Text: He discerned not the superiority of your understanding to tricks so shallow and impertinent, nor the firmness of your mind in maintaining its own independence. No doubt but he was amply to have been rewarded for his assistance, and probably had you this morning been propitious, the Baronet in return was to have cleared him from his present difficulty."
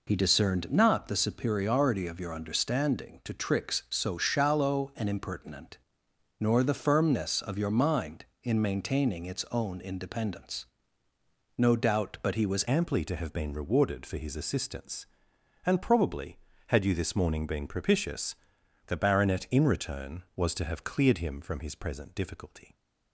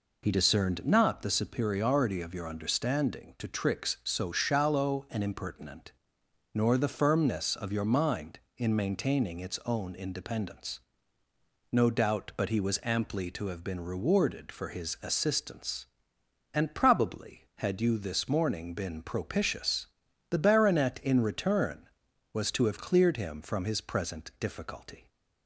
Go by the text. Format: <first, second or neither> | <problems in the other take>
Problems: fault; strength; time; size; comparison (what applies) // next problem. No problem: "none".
second | changes voice at "amply"; from 12.6 s on; 10.1 s long